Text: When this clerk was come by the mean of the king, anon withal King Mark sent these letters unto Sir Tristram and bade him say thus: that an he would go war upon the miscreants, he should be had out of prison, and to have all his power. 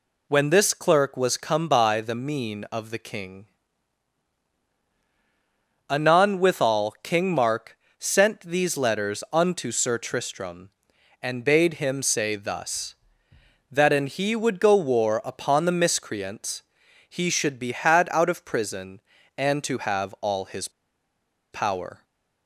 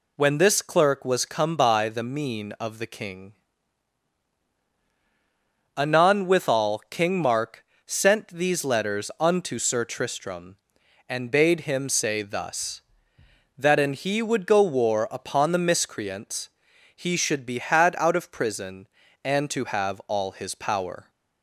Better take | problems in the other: second | pauses between "Mark" and "sent"; slight; at 7.7 s; 0.24 s long; slight in the second // pauses between "his" and "power"; noticeable; at 20.6 s; 0.83 s long // stays silent after the last word; slight; from 21.9 s on; 0.5 s long

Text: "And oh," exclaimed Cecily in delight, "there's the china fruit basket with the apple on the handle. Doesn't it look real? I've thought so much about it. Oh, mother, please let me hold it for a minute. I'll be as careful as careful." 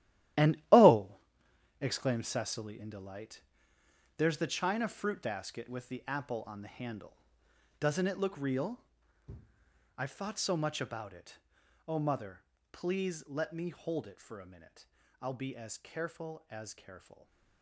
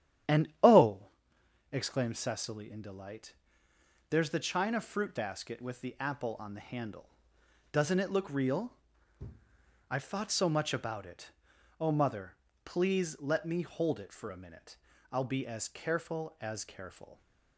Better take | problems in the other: second | gets quieter; strong; throughout; 12 dB // starts louder than the rest; strong; until 2.1 s; 13 dB; strong in the second

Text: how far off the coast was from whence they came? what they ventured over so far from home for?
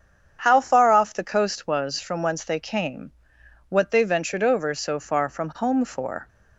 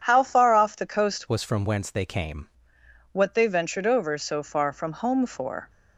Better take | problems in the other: first | starts louder than the rest; strong; until 1.0 s; 8.5 dB; strong in the first // changes voice from "was" to "came"; from 1.2 to 2.4 s; 1.2 s long

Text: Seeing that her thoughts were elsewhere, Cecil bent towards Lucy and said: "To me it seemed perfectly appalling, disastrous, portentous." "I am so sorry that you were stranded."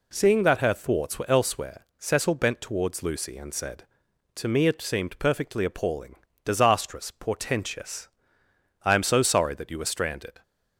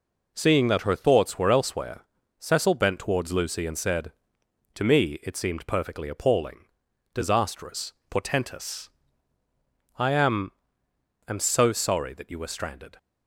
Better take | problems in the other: first | says "am" twice; at 11.2 s

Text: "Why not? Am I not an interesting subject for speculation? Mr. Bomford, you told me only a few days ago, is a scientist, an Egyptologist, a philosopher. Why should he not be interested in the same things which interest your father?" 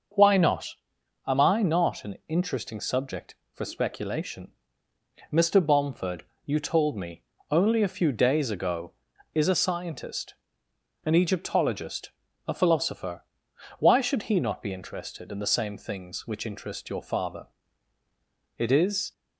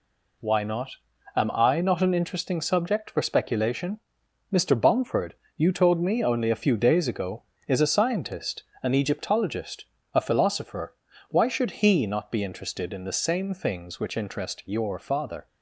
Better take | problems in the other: second | starts louder than the rest; noticeable; until 1.6 s; 6 dB // pauses between "me" and "only"; slight; at 7.2 s; 0.28 s long // goes on to say "It is"; from 18.5 s on; 0.54 s long

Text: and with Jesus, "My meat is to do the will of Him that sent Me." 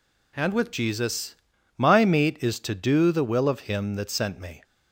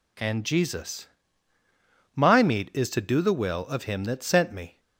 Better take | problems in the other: first | skips "with"; at 0.4 s

